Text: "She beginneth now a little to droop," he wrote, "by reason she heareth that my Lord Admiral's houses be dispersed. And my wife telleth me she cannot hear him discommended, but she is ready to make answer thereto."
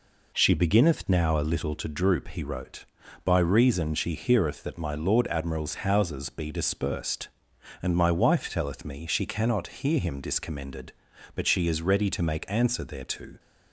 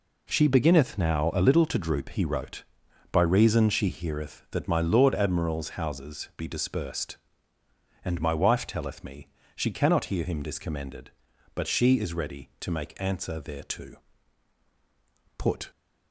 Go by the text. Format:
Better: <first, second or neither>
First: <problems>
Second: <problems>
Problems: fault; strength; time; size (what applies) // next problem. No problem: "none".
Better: first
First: none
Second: pauses between "me" and "she"; slight; at 9.2 s; 0.26 s long // goes on to say "Put"; slight; from 15.3 s on; 0.32 s long